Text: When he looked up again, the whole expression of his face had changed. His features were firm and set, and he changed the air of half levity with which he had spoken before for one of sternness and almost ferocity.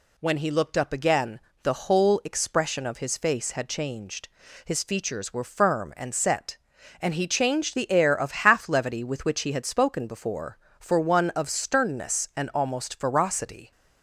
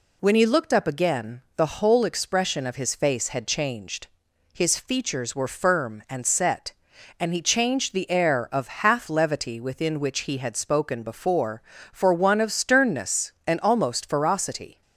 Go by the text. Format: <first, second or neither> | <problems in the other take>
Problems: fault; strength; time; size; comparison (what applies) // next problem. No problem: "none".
first | says "within" for "with"; at 9.6 s